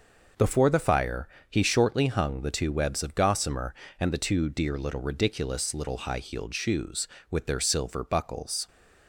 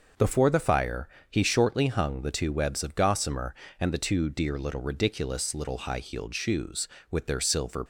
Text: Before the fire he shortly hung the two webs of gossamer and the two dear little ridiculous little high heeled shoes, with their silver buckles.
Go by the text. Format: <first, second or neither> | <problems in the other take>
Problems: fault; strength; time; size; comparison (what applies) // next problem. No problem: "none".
first | pauses between "fire" and "he"; slight; at 1.0 s; 0.20 s long; slight in the first // stops before "buckles"; at 7.8 s